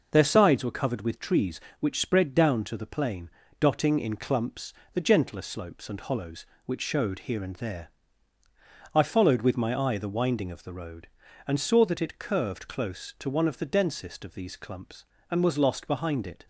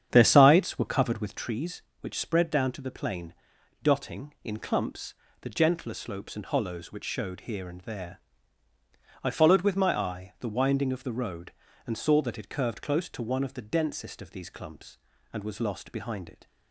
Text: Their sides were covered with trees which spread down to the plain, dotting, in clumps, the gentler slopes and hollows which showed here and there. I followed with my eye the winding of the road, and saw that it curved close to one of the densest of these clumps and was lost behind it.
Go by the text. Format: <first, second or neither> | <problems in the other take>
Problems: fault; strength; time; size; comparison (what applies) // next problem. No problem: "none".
first | starts louder than the rest; strong; until 1.4 s; 8.5 dB